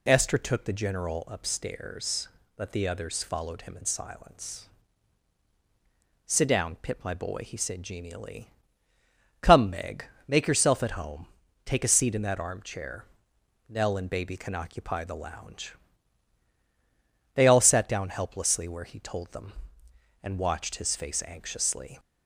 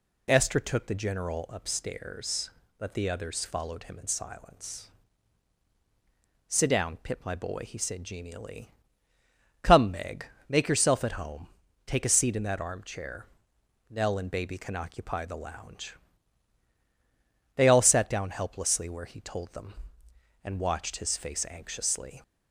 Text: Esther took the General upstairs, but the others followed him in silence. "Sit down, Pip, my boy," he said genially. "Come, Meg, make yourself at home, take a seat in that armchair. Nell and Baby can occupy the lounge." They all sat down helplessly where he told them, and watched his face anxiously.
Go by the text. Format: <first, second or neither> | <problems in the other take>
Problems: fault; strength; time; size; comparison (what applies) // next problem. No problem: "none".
neither | none